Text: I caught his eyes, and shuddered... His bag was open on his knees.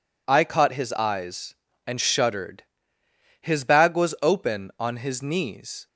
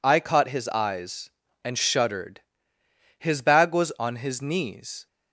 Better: first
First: none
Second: skips "open"; at 3.9 s

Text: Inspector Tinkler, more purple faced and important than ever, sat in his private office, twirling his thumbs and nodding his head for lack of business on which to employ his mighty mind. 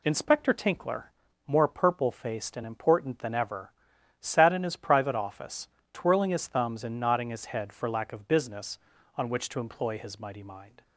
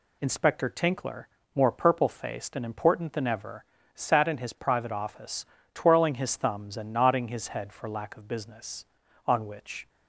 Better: first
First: none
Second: stops before "to employ his mighty mind"; at 9.8 s

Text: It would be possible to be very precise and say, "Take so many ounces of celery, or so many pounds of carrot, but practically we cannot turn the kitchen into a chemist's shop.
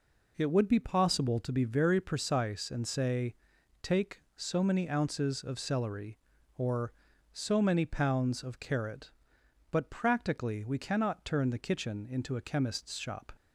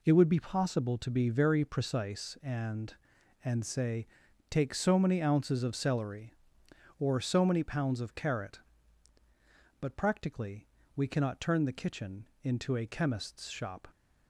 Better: first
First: none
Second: says "and" twice; at 3.4 s // pauses between "practically" and "we"; slight; at 10.6 s; 0.28 s long // pauses between "kitchen" and "into"; slight; at 12.2 s; 0.16 s long

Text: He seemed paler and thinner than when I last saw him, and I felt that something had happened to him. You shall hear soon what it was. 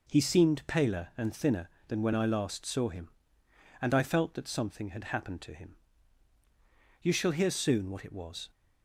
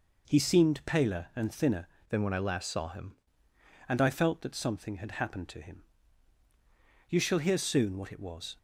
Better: first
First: none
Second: changes voice from "than" to "him"; from 2.0 to 3.1 s; 1.1 s long

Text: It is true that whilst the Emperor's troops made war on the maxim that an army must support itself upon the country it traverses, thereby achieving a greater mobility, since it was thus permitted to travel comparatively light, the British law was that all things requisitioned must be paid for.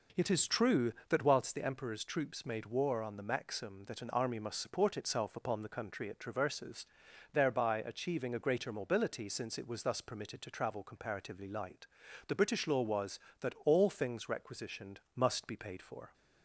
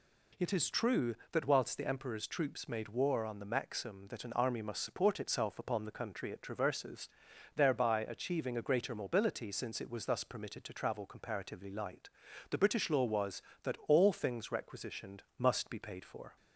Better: second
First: starts louder than the rest; noticeable; until 1.4 s; 5 dB // pauses between "requisitioned" and "must"; slight; at 14.9 s; 0.16 s long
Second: pauses between "requisitioned" and "must"; slight; at 15.2 s; 0.16 s long

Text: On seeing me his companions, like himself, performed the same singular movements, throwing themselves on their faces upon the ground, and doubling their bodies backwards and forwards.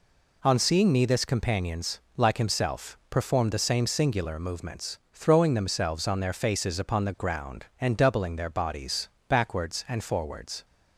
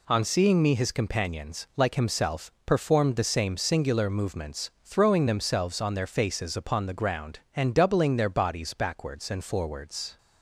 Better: second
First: says "this" for "his"; at 1.0 s // pauses between "bodies" and "backwards"; slight; at 9.0 s; 0.22 s long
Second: none

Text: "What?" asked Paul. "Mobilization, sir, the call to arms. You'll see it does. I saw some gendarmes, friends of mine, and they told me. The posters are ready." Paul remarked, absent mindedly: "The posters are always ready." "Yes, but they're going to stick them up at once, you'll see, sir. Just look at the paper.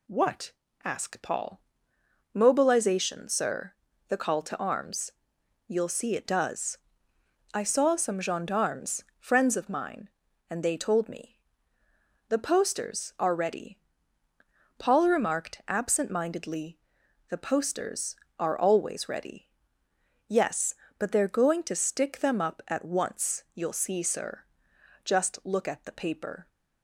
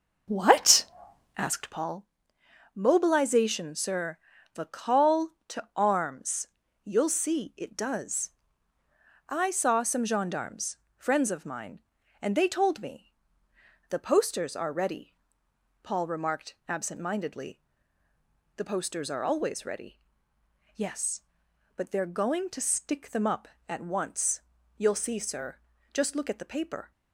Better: first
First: none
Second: starts louder than the rest; noticeable; until 2.0 s; 6 dB

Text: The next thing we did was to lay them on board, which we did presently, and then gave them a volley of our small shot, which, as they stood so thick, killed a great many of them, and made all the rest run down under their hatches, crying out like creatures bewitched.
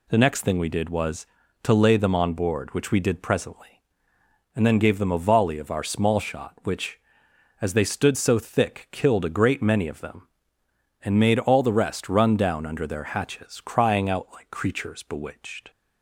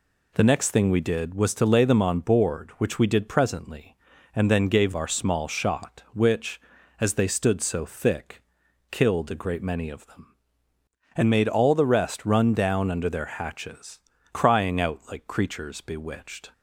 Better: first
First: none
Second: skips "them a volley of"; at 4.9 s

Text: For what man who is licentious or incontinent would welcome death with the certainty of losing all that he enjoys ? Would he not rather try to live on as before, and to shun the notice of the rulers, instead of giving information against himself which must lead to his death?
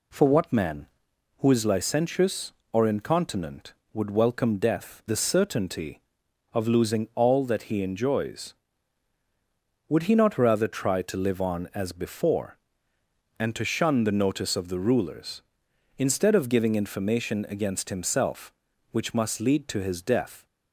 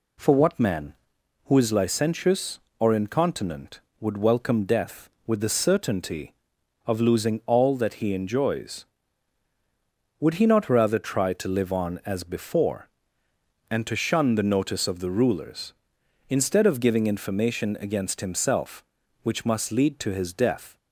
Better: second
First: skips "with"; at 5.0 s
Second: none

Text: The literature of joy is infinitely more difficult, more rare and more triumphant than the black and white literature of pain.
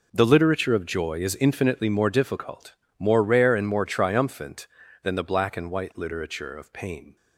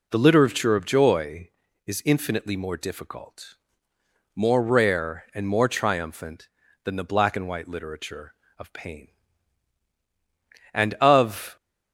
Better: first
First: none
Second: goes on to say "And of"; noticeable; from 10.7 s on; 0.82 s long

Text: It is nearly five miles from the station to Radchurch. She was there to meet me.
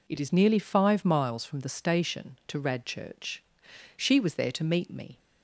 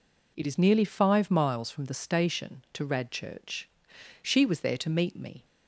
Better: neither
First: none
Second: none

